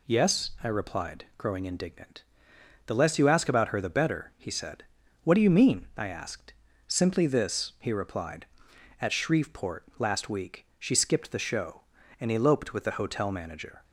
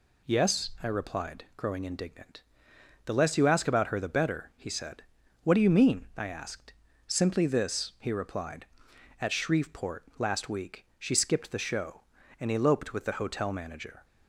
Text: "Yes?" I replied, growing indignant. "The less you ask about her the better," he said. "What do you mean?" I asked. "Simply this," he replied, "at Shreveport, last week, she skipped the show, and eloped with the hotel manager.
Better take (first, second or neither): neither